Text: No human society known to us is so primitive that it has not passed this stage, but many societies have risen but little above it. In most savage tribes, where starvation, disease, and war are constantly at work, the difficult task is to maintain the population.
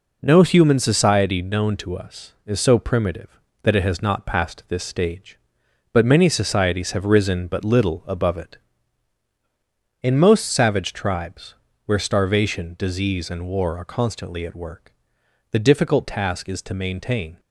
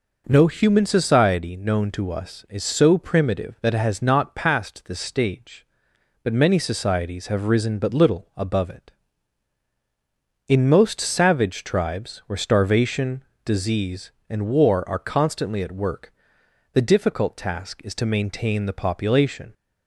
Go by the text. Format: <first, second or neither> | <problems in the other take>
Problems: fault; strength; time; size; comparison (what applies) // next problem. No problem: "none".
second | stops before "the population"; at 17.3 s